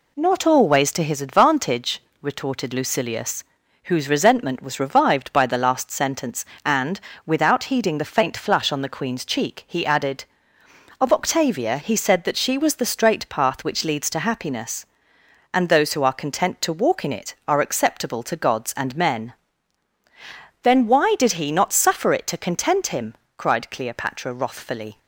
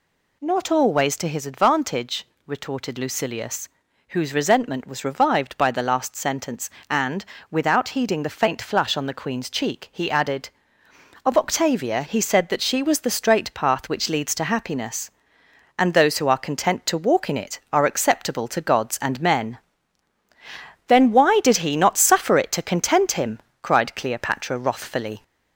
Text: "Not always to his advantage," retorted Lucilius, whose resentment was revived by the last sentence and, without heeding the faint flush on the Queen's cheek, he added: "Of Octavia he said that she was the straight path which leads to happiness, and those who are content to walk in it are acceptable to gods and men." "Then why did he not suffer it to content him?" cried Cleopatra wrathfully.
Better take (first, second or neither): first